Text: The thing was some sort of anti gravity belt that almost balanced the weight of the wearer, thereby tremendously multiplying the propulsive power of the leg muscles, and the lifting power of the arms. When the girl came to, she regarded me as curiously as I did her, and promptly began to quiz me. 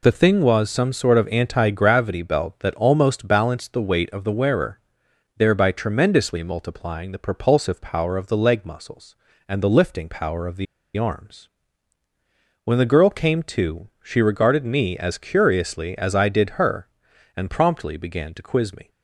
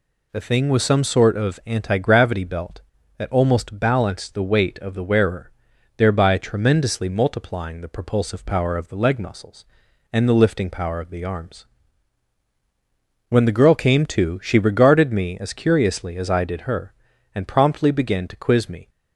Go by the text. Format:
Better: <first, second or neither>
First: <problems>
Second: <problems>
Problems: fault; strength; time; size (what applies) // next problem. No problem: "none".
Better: second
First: pauses between "the" and "arms"; slight; at 10.6 s; 0.31 s long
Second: none